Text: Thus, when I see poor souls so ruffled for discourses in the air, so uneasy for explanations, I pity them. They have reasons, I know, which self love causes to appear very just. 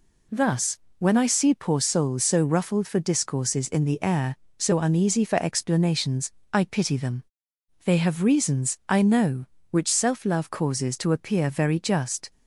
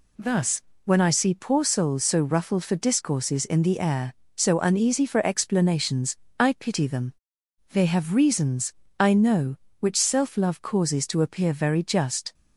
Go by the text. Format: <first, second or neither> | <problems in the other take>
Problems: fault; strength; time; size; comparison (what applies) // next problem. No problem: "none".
neither | none